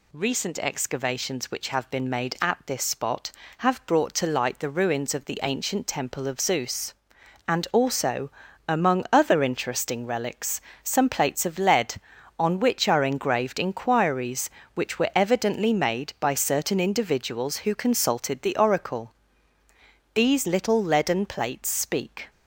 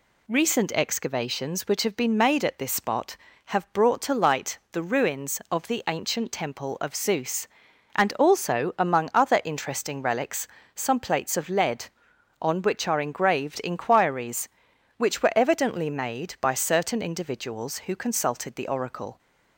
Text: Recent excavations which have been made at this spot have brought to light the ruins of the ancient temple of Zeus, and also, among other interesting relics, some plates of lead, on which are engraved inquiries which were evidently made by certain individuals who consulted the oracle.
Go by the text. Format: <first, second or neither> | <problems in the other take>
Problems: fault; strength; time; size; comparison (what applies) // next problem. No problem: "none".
second | goes on to say "These little leaden plates speak"; strong; from 20.1 s on; 2.1 s long